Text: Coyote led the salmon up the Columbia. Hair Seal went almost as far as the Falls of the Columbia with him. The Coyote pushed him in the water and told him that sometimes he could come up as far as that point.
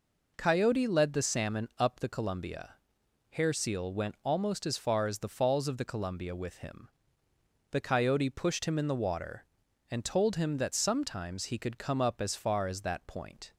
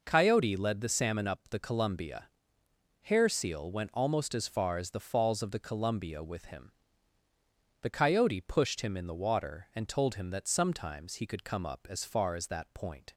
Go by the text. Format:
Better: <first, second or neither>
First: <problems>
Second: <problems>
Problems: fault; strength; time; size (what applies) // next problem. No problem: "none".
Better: neither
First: none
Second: none